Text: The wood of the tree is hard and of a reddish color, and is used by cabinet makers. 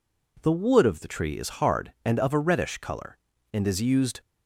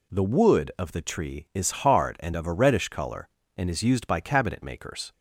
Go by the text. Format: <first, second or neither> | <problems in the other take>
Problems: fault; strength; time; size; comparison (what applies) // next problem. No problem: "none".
second | stops before "by cabinet makers"; at 4.2 s